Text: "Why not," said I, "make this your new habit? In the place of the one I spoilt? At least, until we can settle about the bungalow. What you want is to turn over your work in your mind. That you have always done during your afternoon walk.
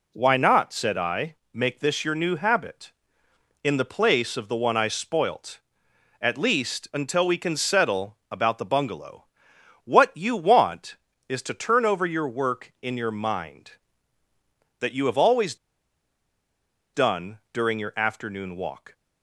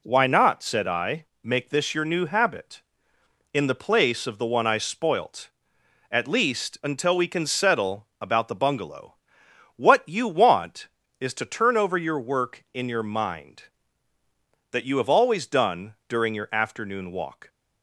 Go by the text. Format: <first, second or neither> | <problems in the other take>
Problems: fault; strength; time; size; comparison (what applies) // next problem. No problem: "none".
second | pauses between "always" and "done"; strong; at 15.5 s; 1.3 s long